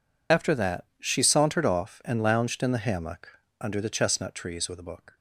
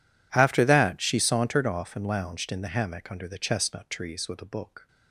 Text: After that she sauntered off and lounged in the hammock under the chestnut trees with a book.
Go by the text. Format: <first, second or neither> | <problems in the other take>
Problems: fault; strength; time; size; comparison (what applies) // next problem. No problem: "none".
second | loses the start of "After"; at 0.3 s; 50 ms // pauses between "hammock" and "under"; slight; at 3.3 s; 0.22 s long